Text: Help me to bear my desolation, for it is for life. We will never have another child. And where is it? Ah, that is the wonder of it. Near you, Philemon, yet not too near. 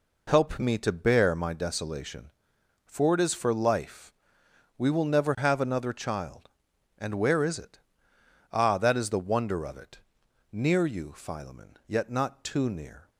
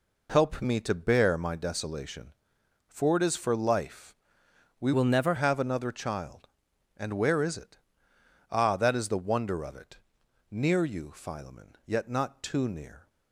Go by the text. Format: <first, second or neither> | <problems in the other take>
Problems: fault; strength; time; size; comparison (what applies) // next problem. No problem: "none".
first | changes voice from "will" to "never"; from 4.9 to 5.3 s; 0.4 s long